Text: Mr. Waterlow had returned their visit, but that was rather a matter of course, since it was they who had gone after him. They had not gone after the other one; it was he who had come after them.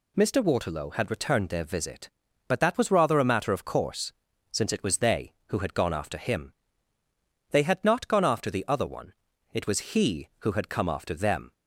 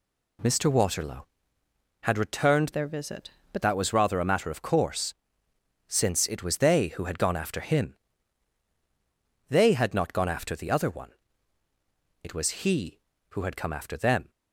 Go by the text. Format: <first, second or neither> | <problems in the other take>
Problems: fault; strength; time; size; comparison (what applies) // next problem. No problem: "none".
first | changes voice from "their" to "but"; from 2.7 to 3.6 s; 0.9 s long